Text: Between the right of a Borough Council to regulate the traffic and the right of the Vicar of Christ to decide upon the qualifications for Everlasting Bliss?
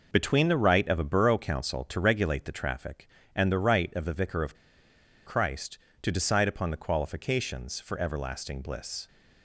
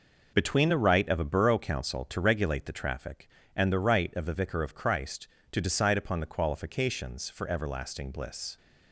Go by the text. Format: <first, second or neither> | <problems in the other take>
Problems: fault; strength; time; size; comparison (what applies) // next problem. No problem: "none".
second | pauses between "of" and "Christ"; noticeable; at 4.5 s; 0.71 s long